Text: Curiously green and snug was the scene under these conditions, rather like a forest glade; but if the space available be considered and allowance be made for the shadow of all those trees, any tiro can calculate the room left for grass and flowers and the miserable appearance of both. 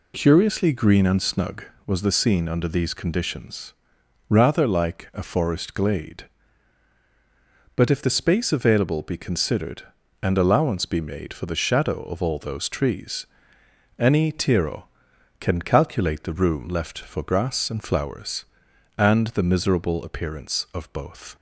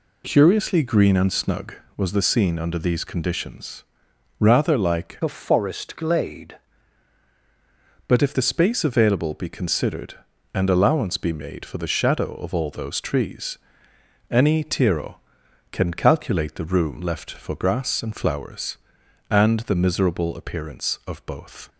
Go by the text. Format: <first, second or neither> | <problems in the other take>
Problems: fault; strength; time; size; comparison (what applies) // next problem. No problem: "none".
first | changes voice from "a" to "glade"; from 5.2 to 6.5 s; 1.3 s long